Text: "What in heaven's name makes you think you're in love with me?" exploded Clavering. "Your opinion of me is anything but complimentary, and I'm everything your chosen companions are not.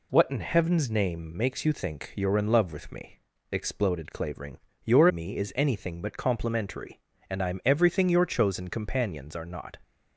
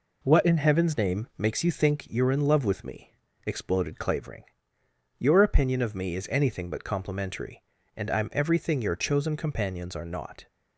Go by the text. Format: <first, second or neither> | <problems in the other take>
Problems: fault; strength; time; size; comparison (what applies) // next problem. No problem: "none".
second | skips "opinion of"; at 5.0 s